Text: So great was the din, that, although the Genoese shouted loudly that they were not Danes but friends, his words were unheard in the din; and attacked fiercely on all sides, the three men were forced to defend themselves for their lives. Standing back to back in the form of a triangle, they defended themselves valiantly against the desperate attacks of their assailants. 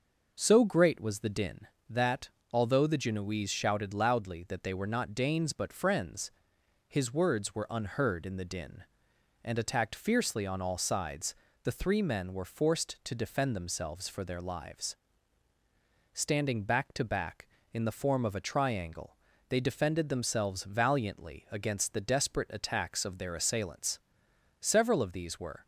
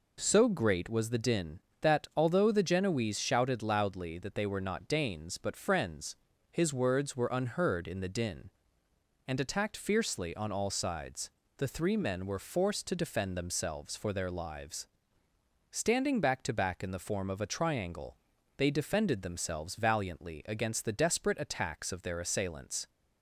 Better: second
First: goes on to say "Several of these were"; noticeable; from 24.7 s on; 0.94 s long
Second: none

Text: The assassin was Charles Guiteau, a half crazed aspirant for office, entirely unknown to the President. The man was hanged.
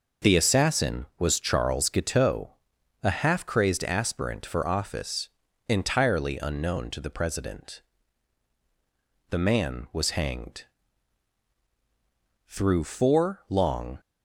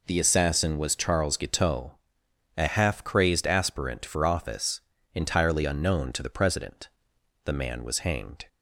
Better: second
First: goes on to say "Through four long"; from 12.4 s on; 1.5 s long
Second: none

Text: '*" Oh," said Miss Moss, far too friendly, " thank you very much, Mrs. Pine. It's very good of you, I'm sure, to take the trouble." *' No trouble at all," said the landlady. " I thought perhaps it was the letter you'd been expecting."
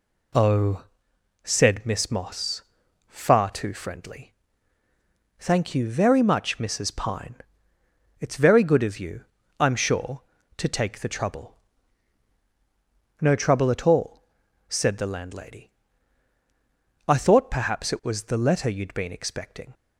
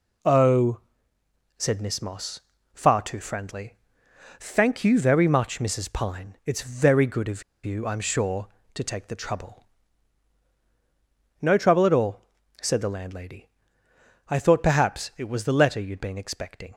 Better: first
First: none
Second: pauses between "of" and "you"; slight; at 7.4 s; 0.23 s long

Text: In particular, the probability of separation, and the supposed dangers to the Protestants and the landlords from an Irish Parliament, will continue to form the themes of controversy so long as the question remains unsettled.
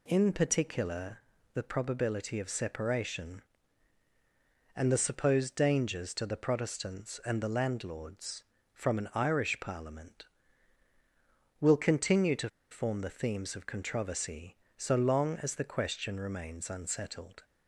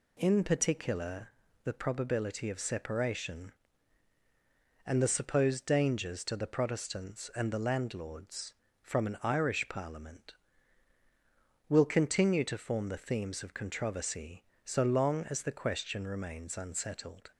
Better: second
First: pauses between "to" and "form"; slight; at 12.4 s; 0.22 s long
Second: none

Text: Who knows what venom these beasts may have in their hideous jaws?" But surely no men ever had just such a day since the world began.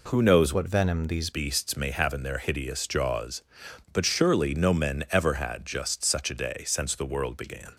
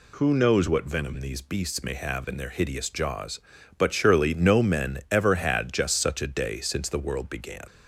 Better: second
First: changes voice from "what" to "these"; from 0.5 to 1.3 s; 0.8 s long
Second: none

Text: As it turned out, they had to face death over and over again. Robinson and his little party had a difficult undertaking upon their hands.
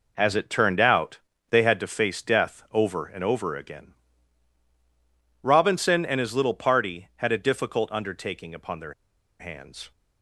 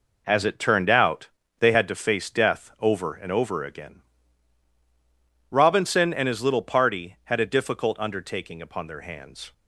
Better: second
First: pauses between "their" and "hands"; noticeable; at 8.9 s; 0.46 s long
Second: none

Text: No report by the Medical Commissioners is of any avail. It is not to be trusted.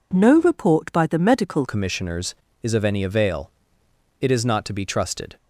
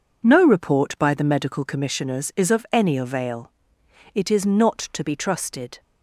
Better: second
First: changes voice at "Commissioners"; from 1.6 s on; 3.7 s long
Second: none

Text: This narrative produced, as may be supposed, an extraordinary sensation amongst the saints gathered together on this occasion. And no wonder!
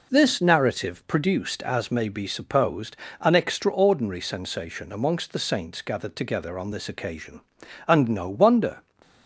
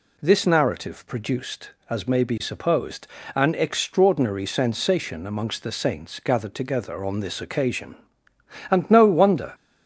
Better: neither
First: none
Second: none

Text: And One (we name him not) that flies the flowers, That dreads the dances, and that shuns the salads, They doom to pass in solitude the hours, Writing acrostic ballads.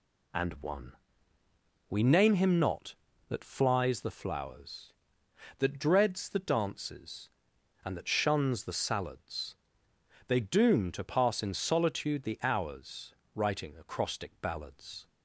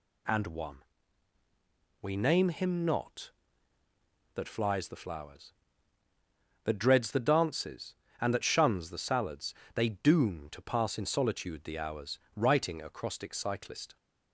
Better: first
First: none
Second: says "cyclist" for "ballads"; at 13.3 s

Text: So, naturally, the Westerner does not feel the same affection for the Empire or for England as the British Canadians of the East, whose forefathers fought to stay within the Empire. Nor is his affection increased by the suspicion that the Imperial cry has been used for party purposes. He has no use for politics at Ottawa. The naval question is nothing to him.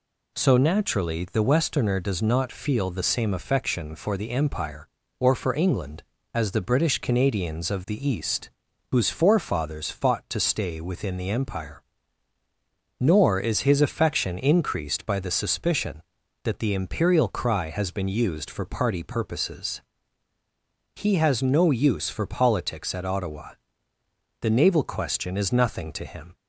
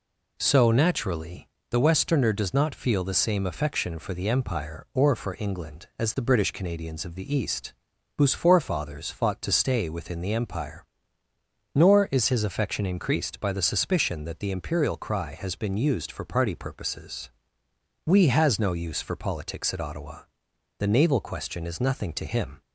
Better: first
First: none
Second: says "We" for "He"; at 18.0 s

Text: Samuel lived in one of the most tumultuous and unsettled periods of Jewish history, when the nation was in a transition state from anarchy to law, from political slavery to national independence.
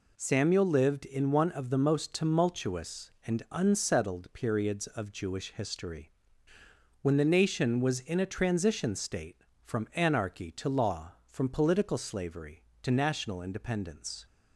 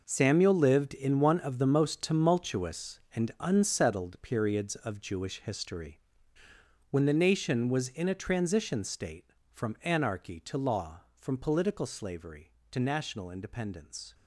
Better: first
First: none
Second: gets quieter; strong; throughout; 12 dB

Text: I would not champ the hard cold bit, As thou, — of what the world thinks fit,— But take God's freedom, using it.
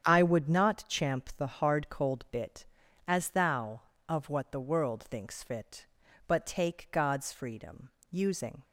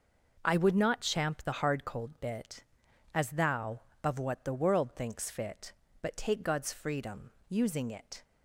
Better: second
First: starts louder than the rest; strong; until 1.1 s; 8.5 dB // stops before "it"; at 8.6 s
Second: none

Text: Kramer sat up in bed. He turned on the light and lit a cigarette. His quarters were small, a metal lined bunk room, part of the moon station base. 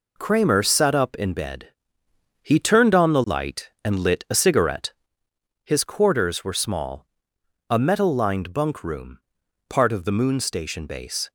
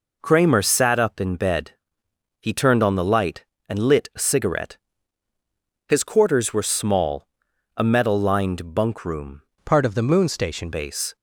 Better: first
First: none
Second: changes voice from "part" to "station"; from 9.6 to 10.7 s; 1.1 s long

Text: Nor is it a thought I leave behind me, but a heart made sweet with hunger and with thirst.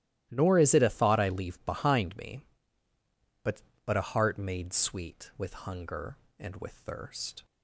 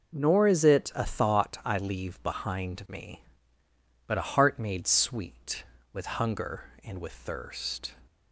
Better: second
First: starts louder than the rest; strong; until 1.3 s; 14.5 dB // says "but" twice; at 3.8 s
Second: none

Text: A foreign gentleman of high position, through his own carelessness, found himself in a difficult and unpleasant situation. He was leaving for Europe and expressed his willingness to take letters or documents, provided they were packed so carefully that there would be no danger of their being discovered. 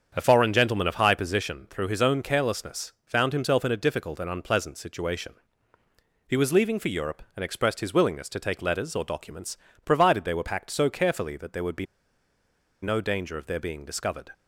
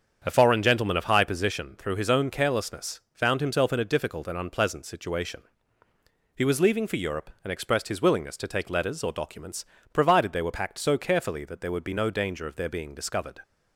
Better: second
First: starts louder than the rest; strong; until 1.1 s; 7.5 dB // pauses between "be" and "no"; at 11.8 s; 0.98 s long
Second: starts louder than the rest; strong; until 1.2 s; 7.5 dB

